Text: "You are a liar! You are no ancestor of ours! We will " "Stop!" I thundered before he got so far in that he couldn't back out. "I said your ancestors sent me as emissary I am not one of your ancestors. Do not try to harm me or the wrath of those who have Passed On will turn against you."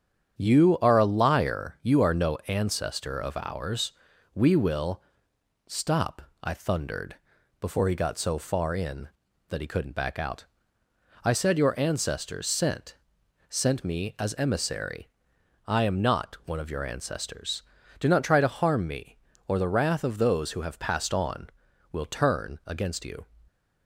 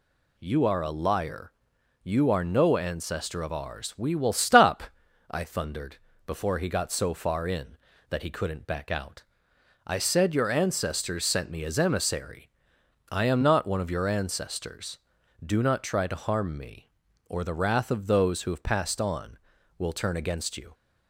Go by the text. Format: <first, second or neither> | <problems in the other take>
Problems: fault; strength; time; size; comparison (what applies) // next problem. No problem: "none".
second | starts louder than the rest; strong; until 1.4 s; 9 dB // pauses between "thundered" and "before"; at 7.1 s; 0.42 s long; slight in the second // says "sent" twice; at 13.4 s // pauses between "emissary" and "I"; noticeable; at 15.0 s; 0.58 s long; noticeable in the second